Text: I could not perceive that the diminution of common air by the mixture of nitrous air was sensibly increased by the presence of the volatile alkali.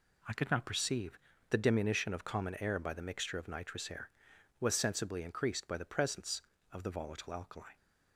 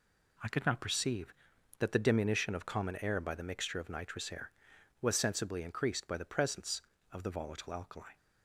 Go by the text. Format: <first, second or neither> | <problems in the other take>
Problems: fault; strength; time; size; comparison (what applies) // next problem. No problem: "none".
second | skips "that"; at 1.3 s